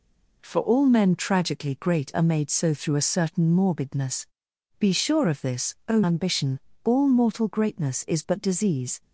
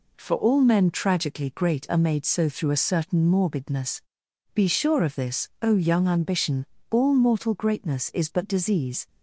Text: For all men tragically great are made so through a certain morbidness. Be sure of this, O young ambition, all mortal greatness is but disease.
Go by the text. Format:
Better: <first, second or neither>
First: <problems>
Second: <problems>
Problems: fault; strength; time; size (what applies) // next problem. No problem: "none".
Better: second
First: skips "young"; at 6.0 s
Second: none